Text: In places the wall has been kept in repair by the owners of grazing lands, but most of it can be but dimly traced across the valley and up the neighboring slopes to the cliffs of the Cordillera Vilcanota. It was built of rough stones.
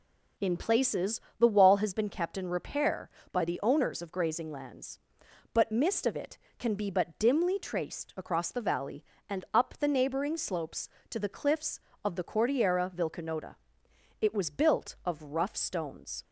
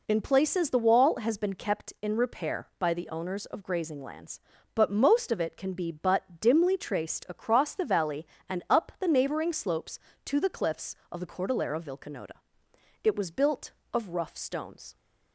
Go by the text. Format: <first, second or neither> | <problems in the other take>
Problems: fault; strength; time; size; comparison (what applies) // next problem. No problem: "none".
second | pauses between "places" and "the"; slight; at 1.1 s; 0.20 s long // says "mist" for "most"; at 5.7 s